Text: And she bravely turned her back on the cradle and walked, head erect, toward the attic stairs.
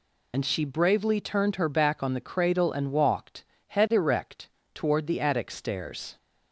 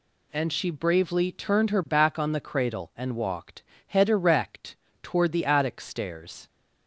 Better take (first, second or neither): second